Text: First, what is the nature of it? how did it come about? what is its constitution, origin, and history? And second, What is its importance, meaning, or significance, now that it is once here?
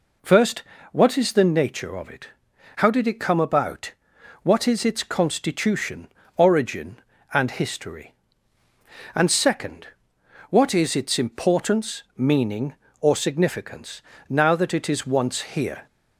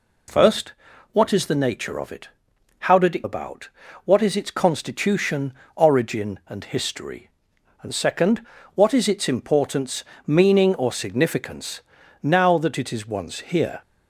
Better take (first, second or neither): first